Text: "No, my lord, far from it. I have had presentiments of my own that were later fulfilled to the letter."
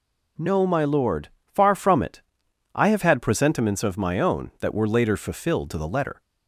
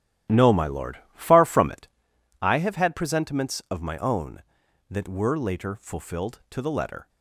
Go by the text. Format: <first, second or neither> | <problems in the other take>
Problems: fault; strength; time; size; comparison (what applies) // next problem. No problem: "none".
first | starts louder than the rest; strong; until 2.1 s; 12 dB